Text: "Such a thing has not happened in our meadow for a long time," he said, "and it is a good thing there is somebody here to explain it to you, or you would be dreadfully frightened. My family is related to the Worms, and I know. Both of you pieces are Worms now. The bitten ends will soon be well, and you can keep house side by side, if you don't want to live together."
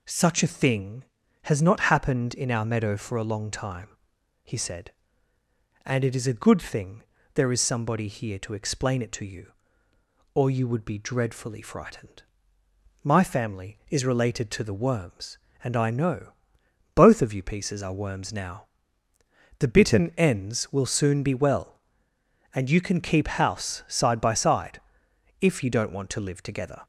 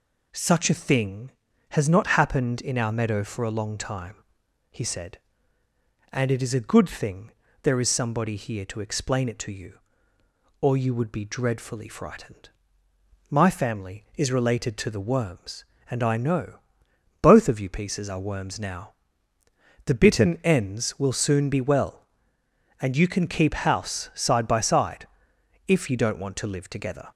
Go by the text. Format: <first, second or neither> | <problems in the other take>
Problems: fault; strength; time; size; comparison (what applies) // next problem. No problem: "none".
neither | pauses between "thing" and "there"; slight; the same in both